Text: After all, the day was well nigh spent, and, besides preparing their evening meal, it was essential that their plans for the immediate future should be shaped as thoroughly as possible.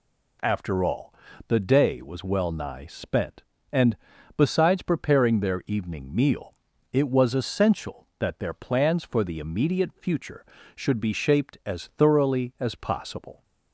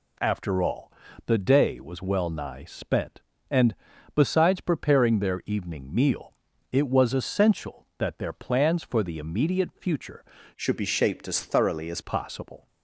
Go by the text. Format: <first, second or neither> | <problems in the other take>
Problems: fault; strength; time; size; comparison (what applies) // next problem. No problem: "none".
first | changes voice from "should" to "as"; from 10.5 to 12.0 s; 1.5 s long